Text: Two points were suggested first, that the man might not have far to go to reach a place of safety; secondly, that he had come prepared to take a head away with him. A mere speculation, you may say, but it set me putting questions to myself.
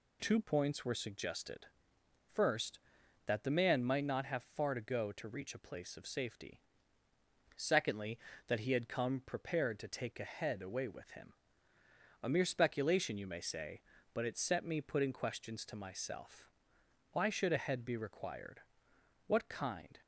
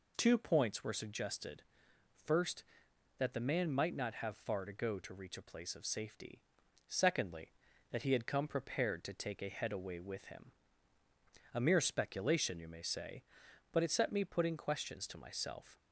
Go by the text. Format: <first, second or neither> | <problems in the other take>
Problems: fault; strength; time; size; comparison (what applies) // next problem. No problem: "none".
second | pauses between "suggested" and "first"; noticeable; at 1.6 s; 0.62 s long; noticeable in the second // goes on to say "Why should a head be required What kind"; strong; from 17.1 s on; 2.8 s long